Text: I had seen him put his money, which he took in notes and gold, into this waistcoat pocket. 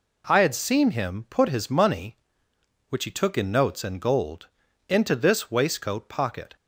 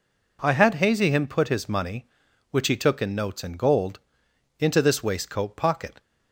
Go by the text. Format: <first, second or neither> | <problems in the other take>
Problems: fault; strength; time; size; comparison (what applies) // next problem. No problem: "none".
first | says "hazy" for "seen"; at 0.7 s